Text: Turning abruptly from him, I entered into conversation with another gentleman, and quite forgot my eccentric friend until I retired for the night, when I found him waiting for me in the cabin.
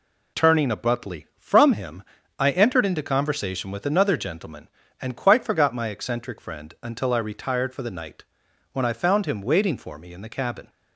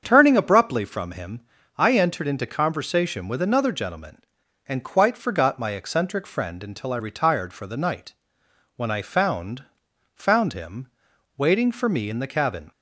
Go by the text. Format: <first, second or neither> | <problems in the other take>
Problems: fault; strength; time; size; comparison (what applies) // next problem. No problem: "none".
first | starts louder than the rest; strong; until 1.0 s; 7.5 dB // says "found" twice; at 10.1 s // pauses between "him" and "waiting"; noticeable; at 10.8 s; 0.48 s long